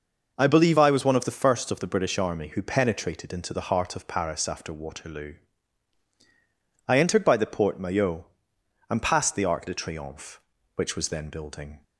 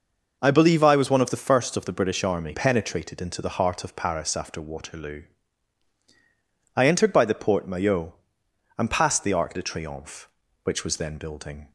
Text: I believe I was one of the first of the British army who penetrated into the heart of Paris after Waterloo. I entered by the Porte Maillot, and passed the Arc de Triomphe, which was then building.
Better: first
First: none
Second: skips "who"; at 2.5 s

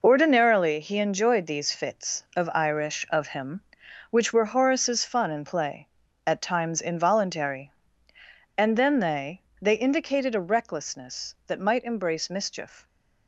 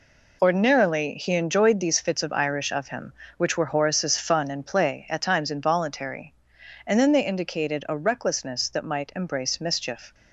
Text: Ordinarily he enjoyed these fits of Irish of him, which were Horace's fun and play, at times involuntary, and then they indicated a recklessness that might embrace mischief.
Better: second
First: says "they" twice; at 9.6 s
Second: none

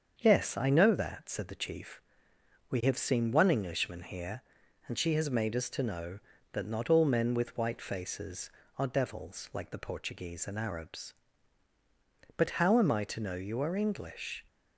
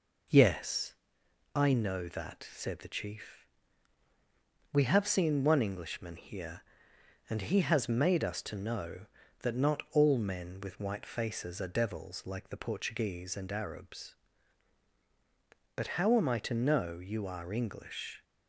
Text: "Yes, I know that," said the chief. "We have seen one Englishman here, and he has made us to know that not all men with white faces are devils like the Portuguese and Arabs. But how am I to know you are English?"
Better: second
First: starts louder than the rest; until 1.2 s; 7 dB // says "she" for "he"; at 4.9 s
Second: none

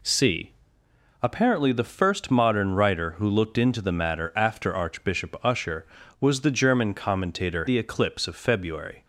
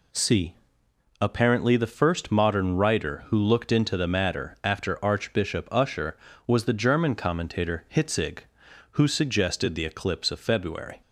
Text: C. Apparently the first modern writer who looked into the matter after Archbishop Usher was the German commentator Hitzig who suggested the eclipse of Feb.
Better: second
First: skips "Hitzig who suggested"; at 7.6 s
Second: none

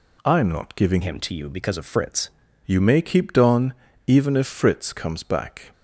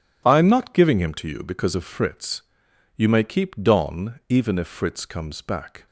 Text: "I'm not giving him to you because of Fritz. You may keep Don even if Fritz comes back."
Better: second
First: changes voice from "him" to "Fritz"; from 1.0 to 2.2 s; 1.2 s long // pauses between "Don" and "even"; slight; at 3.7 s; 0.34 s long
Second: none

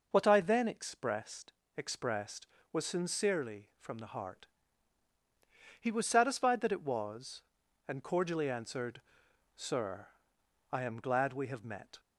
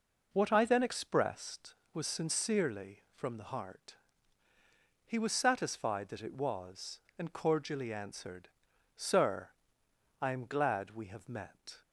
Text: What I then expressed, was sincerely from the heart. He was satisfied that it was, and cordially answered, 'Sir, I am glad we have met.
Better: second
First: says "expressed" twice; at 1.7 s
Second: none

